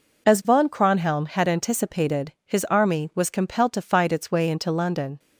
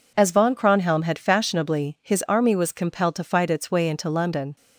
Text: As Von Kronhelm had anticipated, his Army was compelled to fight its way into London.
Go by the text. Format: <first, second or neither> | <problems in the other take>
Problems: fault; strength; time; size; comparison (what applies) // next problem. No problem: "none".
first | says "fashionably" for "anticipated"; at 1.1 s